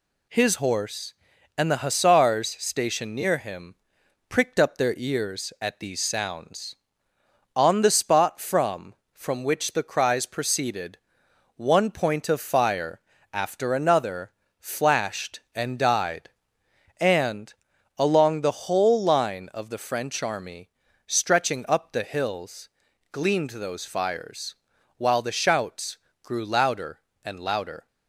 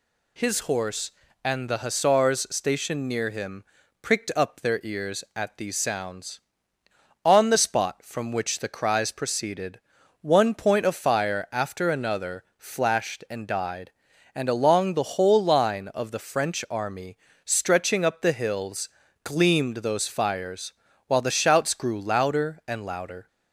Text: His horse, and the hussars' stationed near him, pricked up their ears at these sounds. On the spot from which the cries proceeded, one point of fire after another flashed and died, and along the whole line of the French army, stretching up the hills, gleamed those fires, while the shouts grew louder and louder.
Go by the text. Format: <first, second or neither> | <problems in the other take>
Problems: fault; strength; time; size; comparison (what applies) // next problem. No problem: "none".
second | says "from" twice; at 9.1 s // pauses between "fire" and "after"; slight; at 13.0 s; 0.32 s long // pauses between "another" and "flashed"; slight; at 14.3 s; 0.28 s long; slight in the second // pauses between "and" and "along"; at 17.5 s; 0.44 s long // pauses between "shouts" and "grew"; slight; at 25.9 s; 0.24 s long